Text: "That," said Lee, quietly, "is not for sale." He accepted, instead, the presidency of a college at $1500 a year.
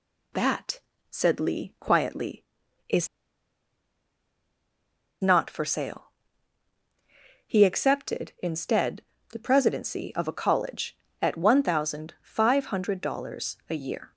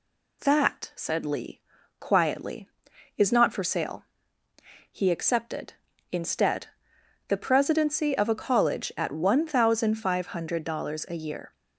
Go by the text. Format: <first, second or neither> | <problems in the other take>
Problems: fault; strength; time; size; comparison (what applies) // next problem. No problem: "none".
second | pauses between "is" and "not"; strong; at 3.0 s; 2.1 s long